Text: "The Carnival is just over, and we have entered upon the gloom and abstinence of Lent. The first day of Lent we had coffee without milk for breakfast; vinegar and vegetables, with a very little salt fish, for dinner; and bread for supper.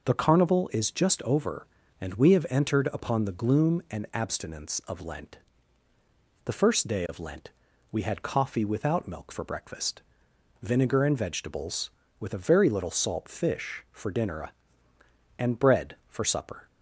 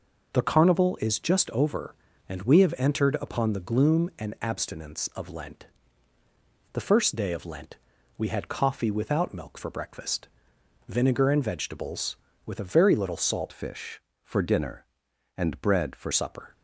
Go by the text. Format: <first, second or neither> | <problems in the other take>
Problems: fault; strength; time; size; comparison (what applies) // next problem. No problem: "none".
first | pauses between "Lent" and "we"; at 7.7 s; 0.42 s long; also in the first // changes voice from "fish" to "for"; from 13.5 to 16.1 s; 2.6 s long